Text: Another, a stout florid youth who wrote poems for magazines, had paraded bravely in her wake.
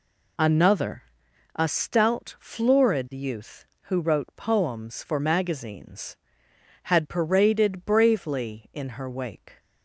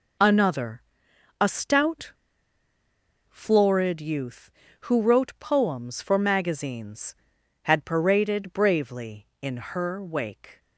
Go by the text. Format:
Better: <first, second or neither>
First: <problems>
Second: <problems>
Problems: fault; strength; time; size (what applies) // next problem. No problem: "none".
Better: first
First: none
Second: pauses between "stout" and "florid"; at 2.1 s; 1.1 s long